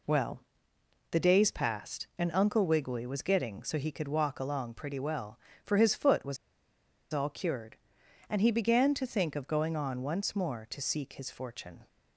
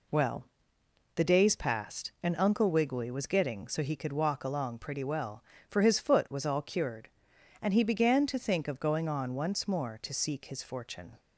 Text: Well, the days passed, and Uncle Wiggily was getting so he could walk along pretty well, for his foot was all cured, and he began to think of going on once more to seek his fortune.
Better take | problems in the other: second | pauses between "was" and "all"; noticeable; at 6.3 s; 0.76 s long

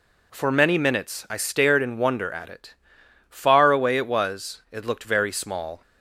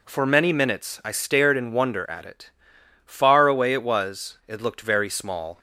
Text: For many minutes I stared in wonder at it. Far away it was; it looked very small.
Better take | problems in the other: neither | none

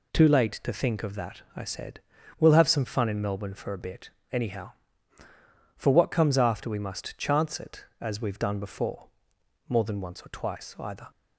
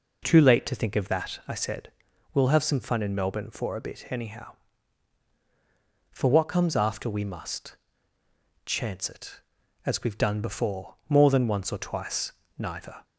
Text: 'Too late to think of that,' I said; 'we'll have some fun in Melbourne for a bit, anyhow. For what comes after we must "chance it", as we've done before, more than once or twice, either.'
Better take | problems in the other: first | pauses between "must" and "chance"; noticeable; at 7.7 s; 0.88 s long // says "neither" for "either"; at 12.5 s

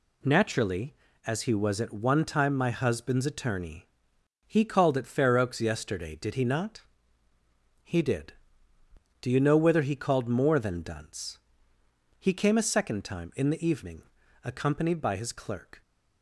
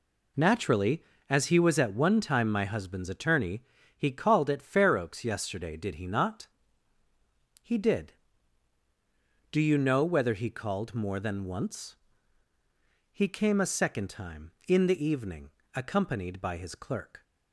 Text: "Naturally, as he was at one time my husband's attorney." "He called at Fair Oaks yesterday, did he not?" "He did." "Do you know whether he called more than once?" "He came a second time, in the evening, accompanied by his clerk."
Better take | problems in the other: second | says "dunce" for "once"; at 10.8 s

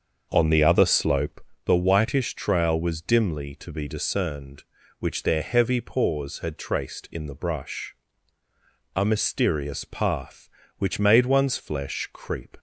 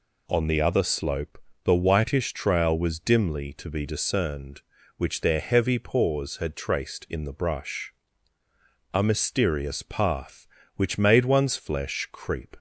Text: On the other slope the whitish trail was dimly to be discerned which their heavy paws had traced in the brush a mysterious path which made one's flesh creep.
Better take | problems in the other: second | starts louder than the rest; until 1.6 s; 6.5 dB // pauses between "slope" and "the"; slight; at 1.4 s; 0.24 s long; slight in the second // pauses between "brush" and "a"; at 7.9 s; 1.0 s long; also in the second

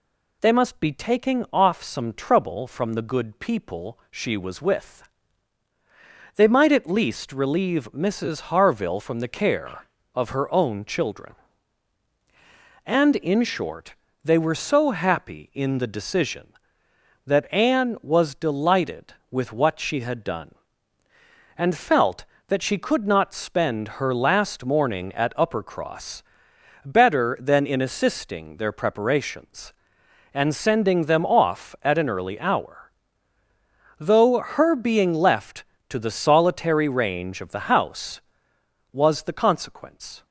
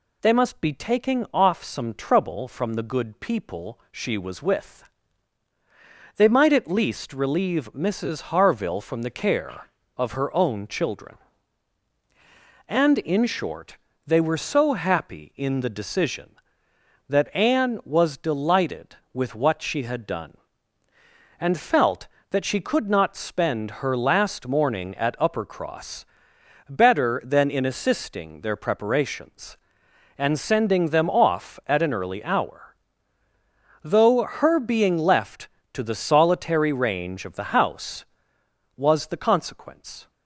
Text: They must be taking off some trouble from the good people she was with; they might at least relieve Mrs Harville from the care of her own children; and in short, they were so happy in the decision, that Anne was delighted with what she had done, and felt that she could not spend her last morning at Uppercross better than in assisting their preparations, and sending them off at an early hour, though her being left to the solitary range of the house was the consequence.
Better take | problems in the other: neither | pauses between "Uppercross" and "better"; noticeable; the same in both

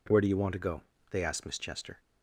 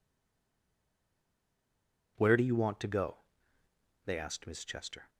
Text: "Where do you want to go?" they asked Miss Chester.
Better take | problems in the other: first | stays silent before the first word; until 2.1 s; 2.1 s long

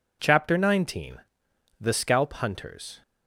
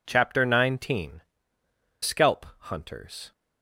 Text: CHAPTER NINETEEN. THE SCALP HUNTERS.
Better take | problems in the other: first | skips "THE"; at 1.6 s // pauses between "SCALP" and "HUNTERS"; slight; at 2.4 s; 0.18 s long

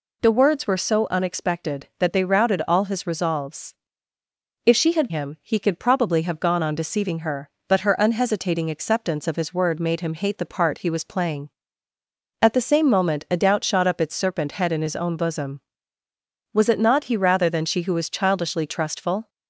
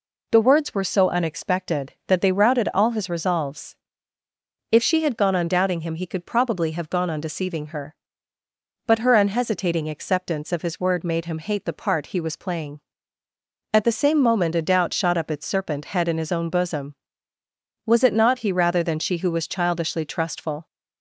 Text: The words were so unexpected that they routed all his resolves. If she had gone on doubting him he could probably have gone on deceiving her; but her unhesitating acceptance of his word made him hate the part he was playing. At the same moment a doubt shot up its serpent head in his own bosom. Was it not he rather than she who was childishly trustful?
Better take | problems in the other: second | skips "gone on doubting"; at 5.0 s

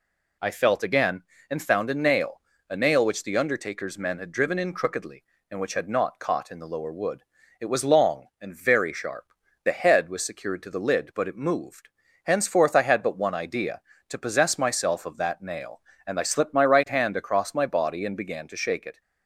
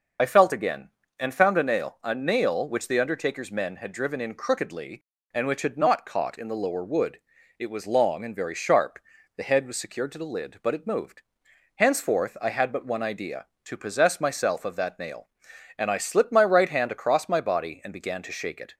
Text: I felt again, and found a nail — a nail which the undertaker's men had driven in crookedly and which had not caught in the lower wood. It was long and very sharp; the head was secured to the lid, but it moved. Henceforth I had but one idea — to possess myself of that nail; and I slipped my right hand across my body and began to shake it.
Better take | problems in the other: first | loses the start of "I"; at 0.1 s; 45 ms

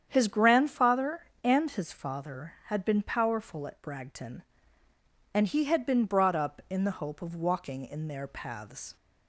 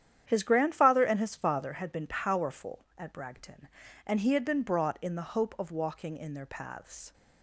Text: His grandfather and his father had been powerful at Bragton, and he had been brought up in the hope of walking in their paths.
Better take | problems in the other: first | starts louder than the rest; strong; until 1.2 s; 10 dB; strong in the first // skips "up"; at 4.9 s

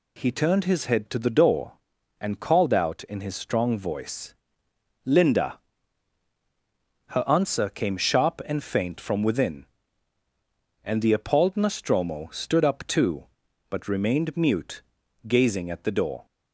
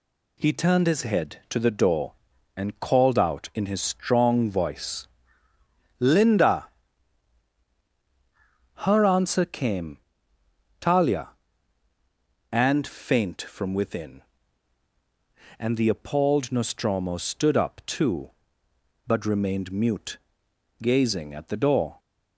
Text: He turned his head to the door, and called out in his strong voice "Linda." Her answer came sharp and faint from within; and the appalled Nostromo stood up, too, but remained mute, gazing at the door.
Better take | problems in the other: first | pauses between "voice" and "Linda"; noticeable; at 5.0 s; 0.94 s long; noticeable in the first // says "talia" for "sharp"; at 10.7 s

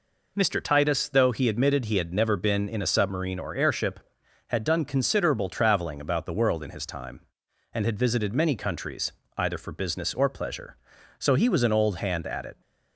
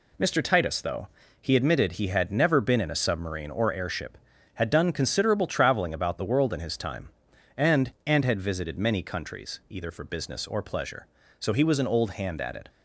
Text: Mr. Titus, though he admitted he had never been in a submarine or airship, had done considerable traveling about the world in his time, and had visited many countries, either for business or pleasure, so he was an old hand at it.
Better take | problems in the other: first | pauses between "though" and "he"; slight; at 1.0 s; 0.32 s long // says "and" twice; at 8.0 s

